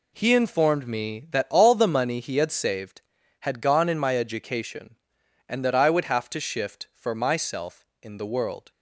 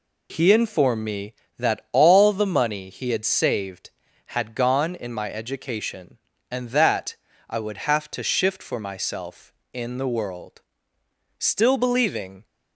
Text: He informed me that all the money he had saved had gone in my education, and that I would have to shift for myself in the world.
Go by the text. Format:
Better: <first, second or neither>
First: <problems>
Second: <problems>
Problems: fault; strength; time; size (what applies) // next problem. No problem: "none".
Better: first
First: none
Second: pauses between "that" and "I"; slight; at 7.1 s; 0.32 s long // goes on to say "Still believing"; noticeable; from 11.3 s on; 1.0 s long